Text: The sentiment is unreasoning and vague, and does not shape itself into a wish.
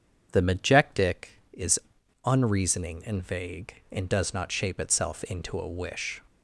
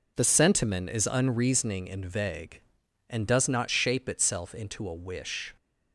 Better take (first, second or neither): second